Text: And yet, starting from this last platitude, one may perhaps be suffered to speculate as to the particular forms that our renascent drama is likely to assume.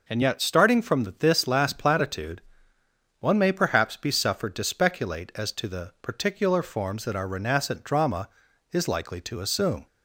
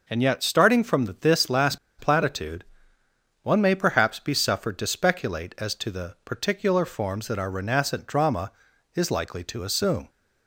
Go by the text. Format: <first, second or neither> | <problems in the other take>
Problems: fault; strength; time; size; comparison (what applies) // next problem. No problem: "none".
first | pauses between "from" and "this"; slight; at 1.0 s; 0.16 s long; slight in the first // pauses between "last" and "platitude"; slight; at 1.7 s; 0.22 s long